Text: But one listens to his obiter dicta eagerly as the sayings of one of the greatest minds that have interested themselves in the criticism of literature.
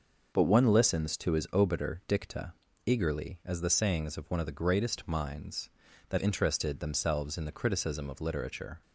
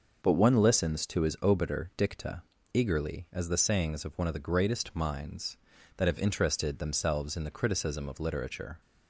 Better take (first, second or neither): second